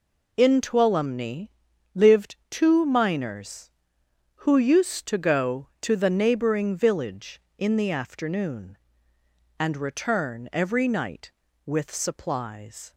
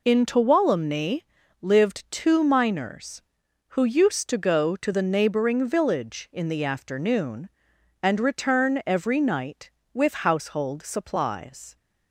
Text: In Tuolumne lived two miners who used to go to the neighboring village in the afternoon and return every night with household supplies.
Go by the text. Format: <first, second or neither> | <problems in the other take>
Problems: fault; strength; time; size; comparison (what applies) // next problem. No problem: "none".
second | pauses between "Tuolumne" and "lived"; at 1.4 s; 0.44 s long; also in the second // skips "household"; at 11.9 s